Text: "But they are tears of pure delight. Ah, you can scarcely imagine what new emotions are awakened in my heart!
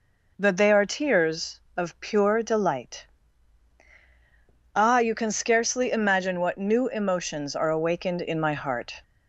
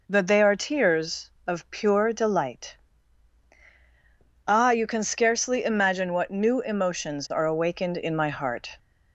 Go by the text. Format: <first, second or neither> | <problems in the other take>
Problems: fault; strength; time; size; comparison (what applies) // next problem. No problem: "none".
neither | none